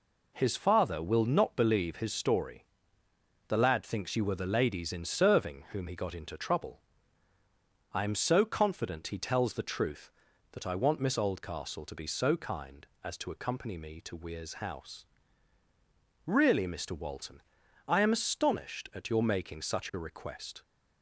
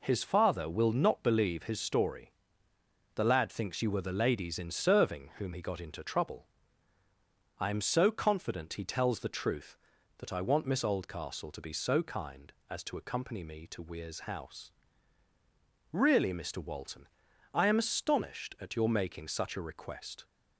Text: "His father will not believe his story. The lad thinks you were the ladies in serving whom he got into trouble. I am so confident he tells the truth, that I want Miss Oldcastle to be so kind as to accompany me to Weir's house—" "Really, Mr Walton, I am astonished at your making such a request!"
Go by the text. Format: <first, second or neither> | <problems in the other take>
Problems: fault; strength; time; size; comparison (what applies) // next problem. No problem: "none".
neither | none